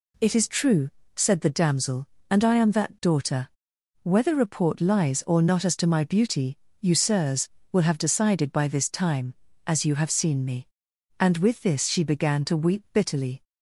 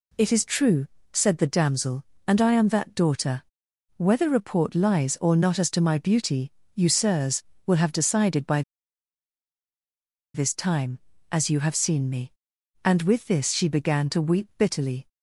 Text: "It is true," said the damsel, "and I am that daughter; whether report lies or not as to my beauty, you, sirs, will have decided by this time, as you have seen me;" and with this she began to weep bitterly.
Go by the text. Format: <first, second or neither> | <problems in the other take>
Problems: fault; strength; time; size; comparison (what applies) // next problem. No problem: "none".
first | pauses between "by" and "this"; strong; at 8.6 s; 1.7 s long